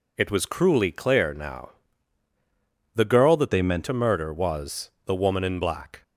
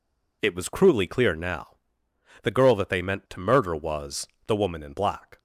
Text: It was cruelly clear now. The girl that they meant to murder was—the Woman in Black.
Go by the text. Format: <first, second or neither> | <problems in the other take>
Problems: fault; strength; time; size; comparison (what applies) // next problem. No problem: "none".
second | changes voice from "they" to "meant"; from 3.5 to 3.8 s; 0.3 s long